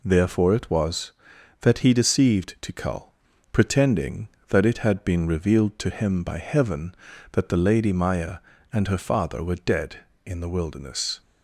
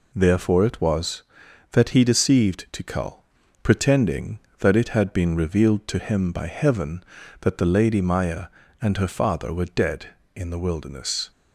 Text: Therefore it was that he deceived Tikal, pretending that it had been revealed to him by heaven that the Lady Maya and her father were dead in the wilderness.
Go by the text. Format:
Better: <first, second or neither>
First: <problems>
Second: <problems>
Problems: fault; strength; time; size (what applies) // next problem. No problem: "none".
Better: neither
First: none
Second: none